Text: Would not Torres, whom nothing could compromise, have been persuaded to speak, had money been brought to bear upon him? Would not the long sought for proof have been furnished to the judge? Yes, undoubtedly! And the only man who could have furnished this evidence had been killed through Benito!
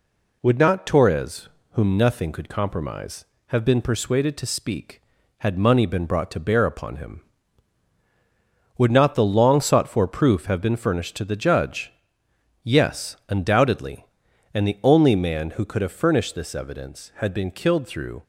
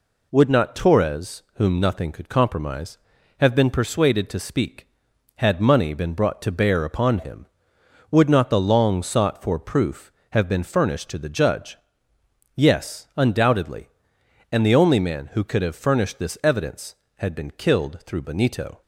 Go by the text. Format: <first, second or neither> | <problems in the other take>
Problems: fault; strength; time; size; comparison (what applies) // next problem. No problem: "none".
second | stops before "Benito"; at 18.2 s